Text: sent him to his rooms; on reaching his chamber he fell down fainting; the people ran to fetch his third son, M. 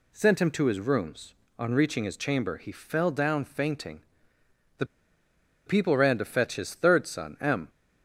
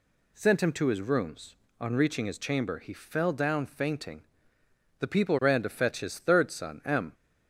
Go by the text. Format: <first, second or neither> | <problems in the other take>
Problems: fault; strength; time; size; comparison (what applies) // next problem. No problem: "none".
second | pauses between "the" and "people"; noticeable; at 4.8 s; 0.81 s long